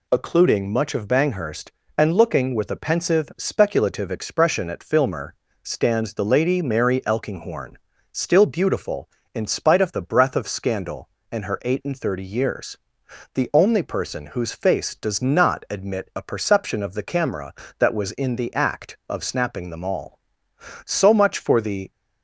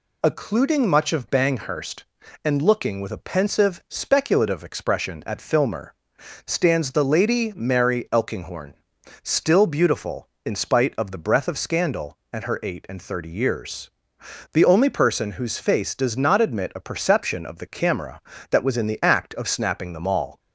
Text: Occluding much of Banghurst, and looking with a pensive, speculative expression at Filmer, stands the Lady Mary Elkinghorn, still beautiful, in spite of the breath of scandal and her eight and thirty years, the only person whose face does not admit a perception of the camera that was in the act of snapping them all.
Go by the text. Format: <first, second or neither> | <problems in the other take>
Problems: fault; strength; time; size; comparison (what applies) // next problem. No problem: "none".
second | goes on to say "So much for the"; noticeable; from 20.8 s on; 1.0 s long